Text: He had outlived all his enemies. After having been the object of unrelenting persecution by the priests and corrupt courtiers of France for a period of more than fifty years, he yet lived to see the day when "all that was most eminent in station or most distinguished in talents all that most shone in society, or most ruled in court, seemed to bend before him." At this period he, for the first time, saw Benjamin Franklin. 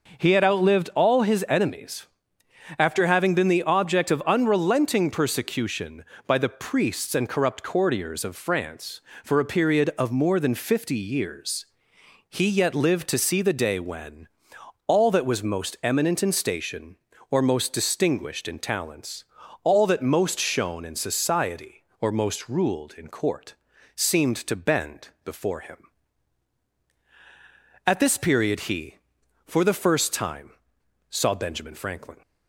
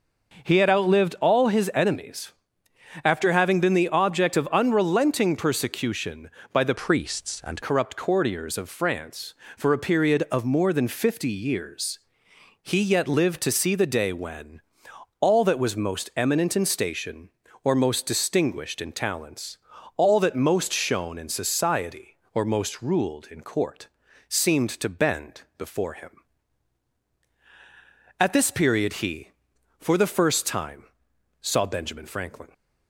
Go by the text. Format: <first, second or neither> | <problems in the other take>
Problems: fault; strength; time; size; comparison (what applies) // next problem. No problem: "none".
first | changes voice from "priests" to "and"; from 6.7 to 7.6 s; 0.9 s long // pauses between "when" and "all"; noticeable; at 14.5 s; 0.62 s long; noticeable in the first // pauses between "talents" and "all"; at 19.5 s; 0.38 s long; also in the first // pauses between "bend" and "before"; slight; at 25.4 s; 0.16 s long; slight in the first